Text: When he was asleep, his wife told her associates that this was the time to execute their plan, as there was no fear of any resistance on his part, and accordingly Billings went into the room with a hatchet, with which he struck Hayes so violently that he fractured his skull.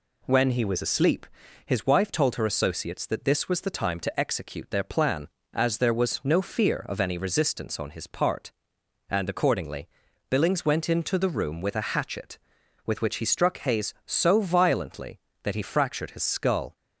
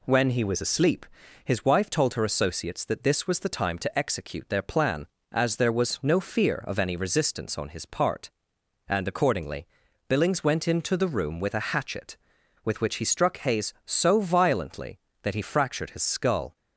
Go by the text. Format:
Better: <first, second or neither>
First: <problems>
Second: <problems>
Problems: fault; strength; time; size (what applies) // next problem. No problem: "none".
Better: neither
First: pauses between "accordingly" and "Billings"; at 9.8 s; 0.40 s long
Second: pauses between "accordingly" and "Billings"; at 9.6 s; 0.40 s long